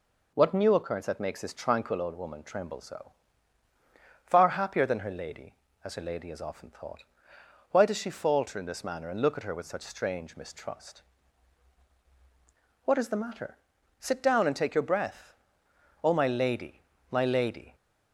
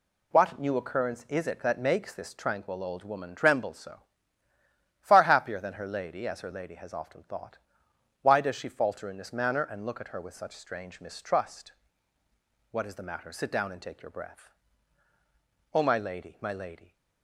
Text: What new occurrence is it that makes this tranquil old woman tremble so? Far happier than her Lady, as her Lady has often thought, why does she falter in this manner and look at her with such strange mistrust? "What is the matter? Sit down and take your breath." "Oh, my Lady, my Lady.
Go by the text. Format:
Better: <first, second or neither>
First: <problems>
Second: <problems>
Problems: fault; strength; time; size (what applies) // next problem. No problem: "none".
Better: second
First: skips "is it"; at 1.0 s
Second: none